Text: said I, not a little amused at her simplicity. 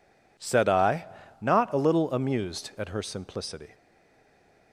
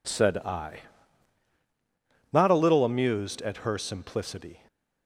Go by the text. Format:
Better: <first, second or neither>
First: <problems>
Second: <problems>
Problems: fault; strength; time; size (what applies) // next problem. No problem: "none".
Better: second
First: stays silent after the last word; from 3.7 s on; 1.0 s long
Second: none